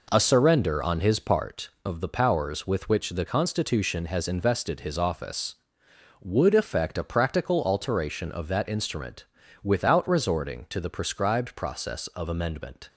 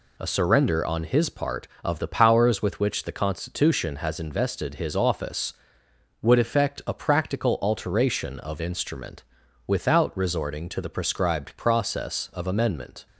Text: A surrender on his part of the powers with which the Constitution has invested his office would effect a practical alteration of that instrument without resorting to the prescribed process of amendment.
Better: first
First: pauses between "instrument" and "without"; at 9.2 s; 0.38 s long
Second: skips "that"; at 8.6 s // pauses between "instrument" and "without"; at 9.2 s; 0.44 s long

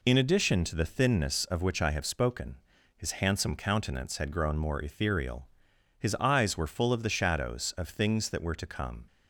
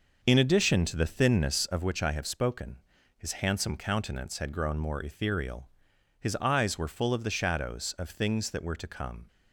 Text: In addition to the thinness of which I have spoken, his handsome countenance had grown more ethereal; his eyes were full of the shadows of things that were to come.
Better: first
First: none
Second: starts louder than the rest; noticeable; until 1.8 s; 6 dB

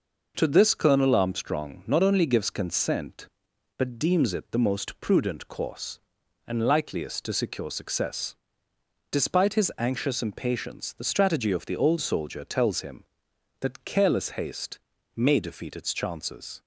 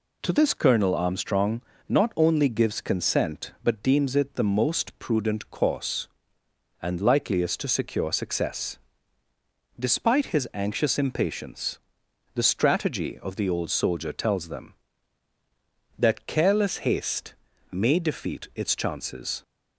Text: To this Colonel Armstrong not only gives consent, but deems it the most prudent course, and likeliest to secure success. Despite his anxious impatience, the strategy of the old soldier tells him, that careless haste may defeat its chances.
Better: first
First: pauses between "haste" and "may"; at 14.7 s; 0.38 s long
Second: pauses between "Armstrong" and "not"; slight; at 1.6 s; 0.26 s long // says "them" for "him"; at 14.4 s // pauses between "haste" and "may"; at 17.3 s; 0.38 s long

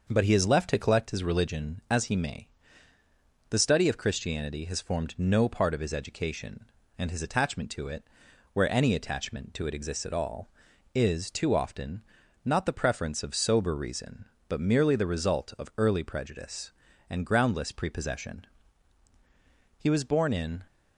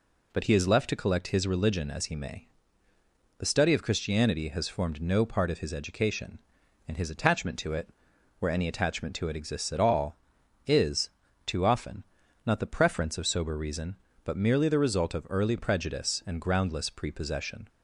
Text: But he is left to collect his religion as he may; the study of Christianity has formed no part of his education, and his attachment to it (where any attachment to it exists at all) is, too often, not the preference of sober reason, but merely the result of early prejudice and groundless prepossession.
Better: second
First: starts louder than the rest; noticeable; until 1.1 s; 6 dB // goes on to say "He was born in"; noticeable; from 19.7 s on; 0.84 s long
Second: none

